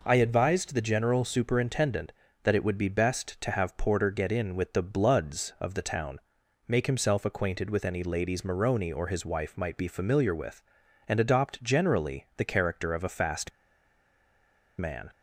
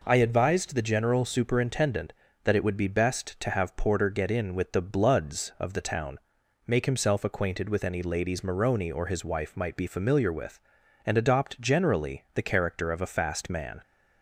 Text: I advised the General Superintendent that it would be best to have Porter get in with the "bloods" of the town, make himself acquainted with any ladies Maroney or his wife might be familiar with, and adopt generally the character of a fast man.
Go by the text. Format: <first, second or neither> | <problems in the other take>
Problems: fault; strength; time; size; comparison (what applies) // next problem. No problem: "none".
second | pauses between "fast" and "man"; strong; at 13.5 s; 1.2 s long